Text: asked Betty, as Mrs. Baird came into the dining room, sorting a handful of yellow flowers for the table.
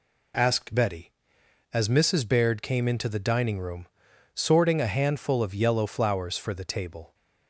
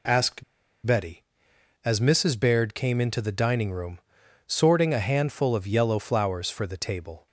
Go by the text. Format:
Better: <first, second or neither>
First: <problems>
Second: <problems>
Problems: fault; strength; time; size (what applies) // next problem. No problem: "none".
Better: first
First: none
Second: pauses between "asked" and "Betty"; at 0.4 s; 0.42 s long